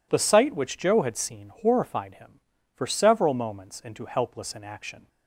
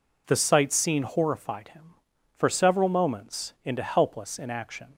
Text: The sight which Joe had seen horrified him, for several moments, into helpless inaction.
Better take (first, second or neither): first